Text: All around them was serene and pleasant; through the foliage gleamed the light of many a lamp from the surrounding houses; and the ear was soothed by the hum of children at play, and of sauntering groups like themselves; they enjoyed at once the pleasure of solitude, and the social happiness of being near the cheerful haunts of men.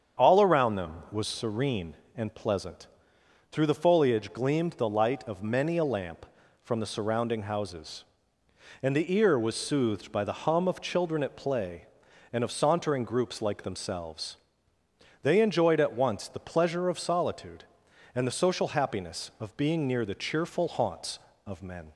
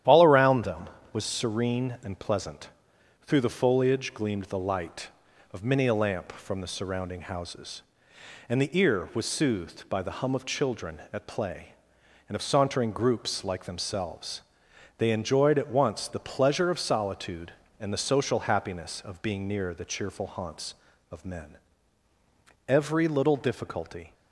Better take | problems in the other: first | starts louder than the rest; strong; until 1.3 s; 11 dB; strong in the first // goes on to say "Every little difficulty"; from 22.6 s on; 1.4 s long

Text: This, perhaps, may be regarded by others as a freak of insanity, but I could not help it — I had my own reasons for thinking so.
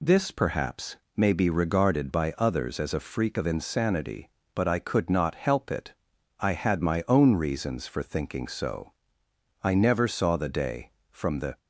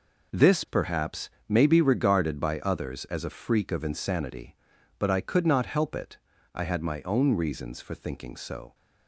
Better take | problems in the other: second | goes on to say "I never saw the day from the"; strong; from 9.6 s on; 1.9 s long

